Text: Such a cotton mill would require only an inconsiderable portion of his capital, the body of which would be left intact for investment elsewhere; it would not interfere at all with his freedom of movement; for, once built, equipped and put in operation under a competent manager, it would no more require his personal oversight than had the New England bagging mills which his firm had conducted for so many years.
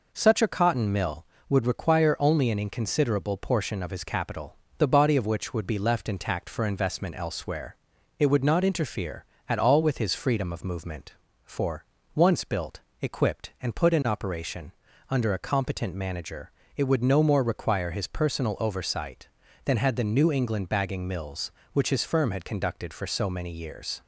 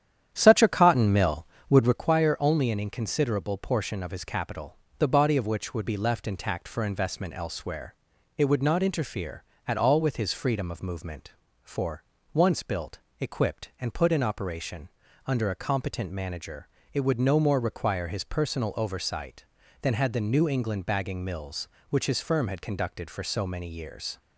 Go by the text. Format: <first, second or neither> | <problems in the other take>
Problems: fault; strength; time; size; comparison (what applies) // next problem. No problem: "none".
first | starts louder than the rest; strong; until 2.1 s; 10 dB // pauses between "operation" and "under"; at 14.8 s; 0.38 s long; also in the first